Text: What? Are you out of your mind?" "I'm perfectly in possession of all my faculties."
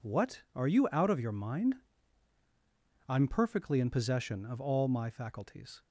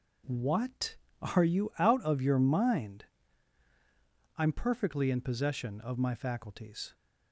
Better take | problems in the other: first | skips "all"; at 5.9 s

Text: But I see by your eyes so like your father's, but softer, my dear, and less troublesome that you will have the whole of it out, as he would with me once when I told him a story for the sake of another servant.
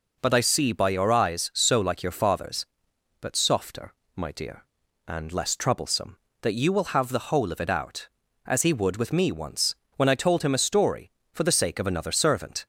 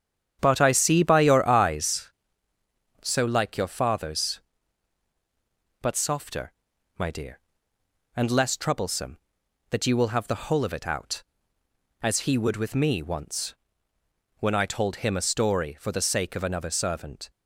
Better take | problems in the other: first | starts louder than the rest; strong; until 2.2 s; 9 dB // pauses between "once" and "when"; noticeable; at 13.5 s; 0.84 s long; slight in the first

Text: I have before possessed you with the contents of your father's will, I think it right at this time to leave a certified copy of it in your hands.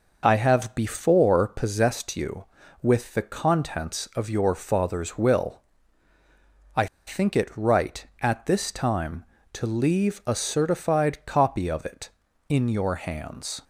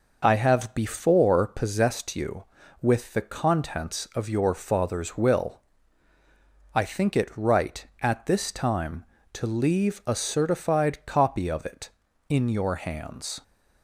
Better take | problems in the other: second | pauses between "I" and "think"; slight; at 6.8 s; 0.20 s long

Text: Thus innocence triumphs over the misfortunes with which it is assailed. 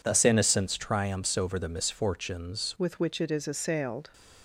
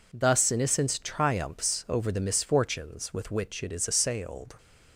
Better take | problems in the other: second | changes voice at "with"; from 2.7 s on; 1.3 s long

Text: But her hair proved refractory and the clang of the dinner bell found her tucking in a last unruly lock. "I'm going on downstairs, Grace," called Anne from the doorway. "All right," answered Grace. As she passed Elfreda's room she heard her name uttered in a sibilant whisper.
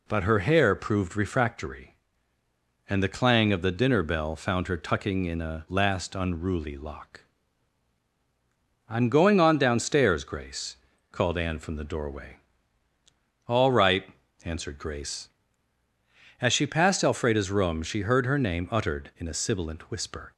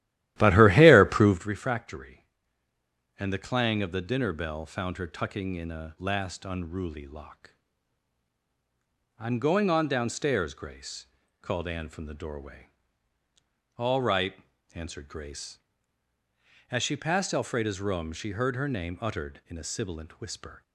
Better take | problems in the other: first | starts louder than the rest; strong; until 1.5 s; 14 dB

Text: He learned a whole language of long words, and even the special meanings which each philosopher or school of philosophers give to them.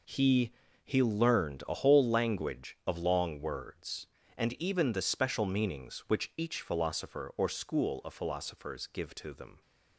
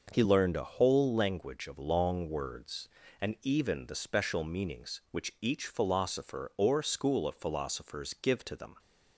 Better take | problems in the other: second | says "He" twice; at 0.8 s

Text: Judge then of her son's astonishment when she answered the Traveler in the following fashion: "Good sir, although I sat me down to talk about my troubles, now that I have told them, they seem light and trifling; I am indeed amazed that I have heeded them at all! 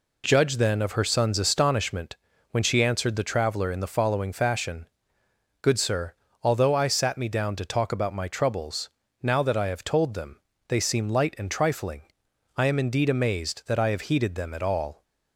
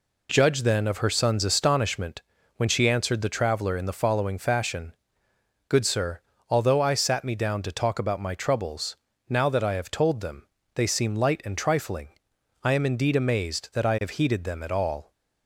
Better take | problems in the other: neither | pauses between "astonishment" and "when"; slight; the same in both

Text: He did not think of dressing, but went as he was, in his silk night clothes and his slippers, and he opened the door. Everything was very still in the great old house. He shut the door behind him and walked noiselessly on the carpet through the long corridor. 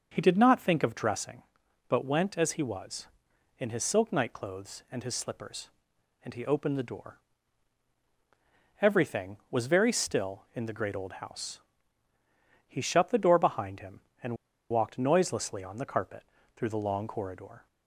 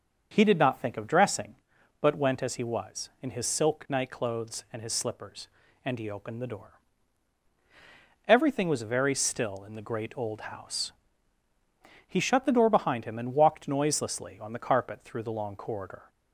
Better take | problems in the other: second | starts louder than the rest; until 1.1 s; 6 dB; also in the second // pauses between "and" and "walked"; slight; at 14.3 s; 0.34 s long // pauses between "carpet" and "through"; slight; at 16.2 s; 0.32 s long

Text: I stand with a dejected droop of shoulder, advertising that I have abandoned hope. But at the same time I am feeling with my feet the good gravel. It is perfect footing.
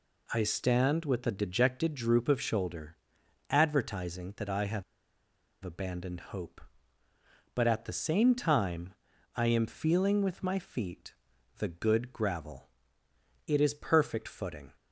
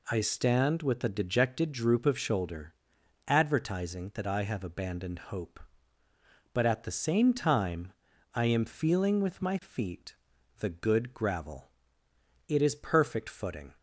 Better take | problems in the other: second | pauses between "have" and "abandoned"; noticeable; at 4.8 s; 0.80 s long // pauses between "time" and "I"; at 8.9 s; 0.42 s long; also in the second // pauses between "feet" and "the"; noticeable; at 11.1 s; 0.46 s long; noticeable in the second

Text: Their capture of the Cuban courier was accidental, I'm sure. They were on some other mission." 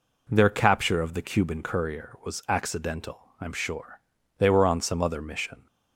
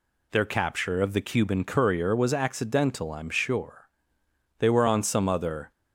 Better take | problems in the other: first | stops before "mission"; at 5.7 s

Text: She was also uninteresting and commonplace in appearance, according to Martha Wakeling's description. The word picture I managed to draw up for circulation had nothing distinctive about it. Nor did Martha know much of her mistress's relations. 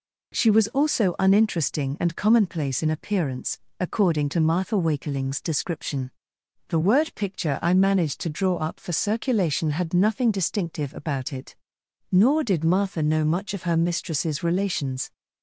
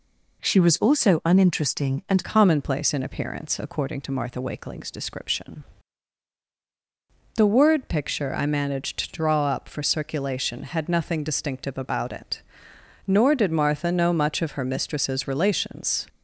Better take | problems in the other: first | changes voice at "commonplace"; from 2.2 s on; 13.8 s long

